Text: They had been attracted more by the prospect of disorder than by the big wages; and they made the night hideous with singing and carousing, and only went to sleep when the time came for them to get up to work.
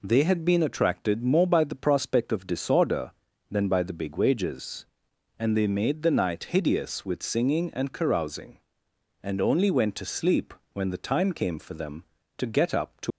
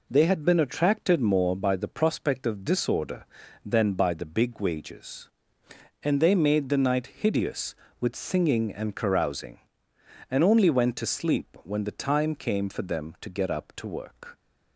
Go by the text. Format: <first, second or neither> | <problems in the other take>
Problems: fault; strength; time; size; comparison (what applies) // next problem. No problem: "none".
second | pauses between "sleep" and "when"; slight; at 10.5 s; 0.18 s long // stops before "work"; at 13.1 s